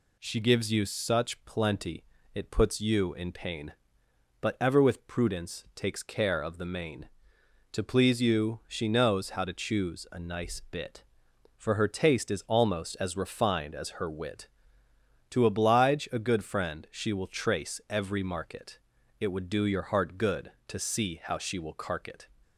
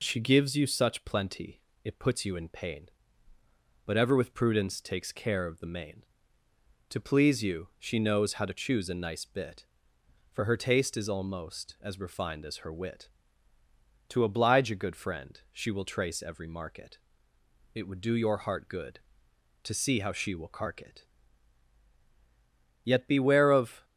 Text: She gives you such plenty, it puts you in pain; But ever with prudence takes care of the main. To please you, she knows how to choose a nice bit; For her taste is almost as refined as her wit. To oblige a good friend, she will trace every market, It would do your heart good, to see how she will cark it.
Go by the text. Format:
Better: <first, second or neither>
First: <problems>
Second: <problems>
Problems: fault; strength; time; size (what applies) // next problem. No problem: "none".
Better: first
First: none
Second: goes on to say "Yet beware of"; noticeable; from 22.8 s on; 1.0 s long